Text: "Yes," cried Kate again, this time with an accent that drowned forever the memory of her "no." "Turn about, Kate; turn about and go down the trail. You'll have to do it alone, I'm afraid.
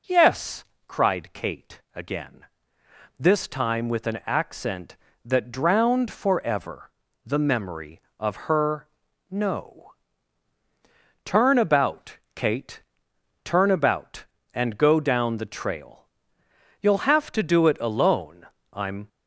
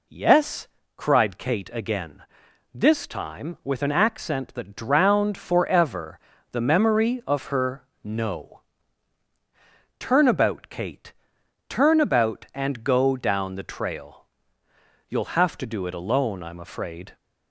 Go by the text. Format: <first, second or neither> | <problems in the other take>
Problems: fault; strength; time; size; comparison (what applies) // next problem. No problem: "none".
second | pauses between "forever" and "the"; slight; at 6.8 s; 0.34 s long; slight in the second // pauses between "her" and "no"; at 8.8 s; 0.42 s long; slight in the second // stops before "afraid"; at 19.0 s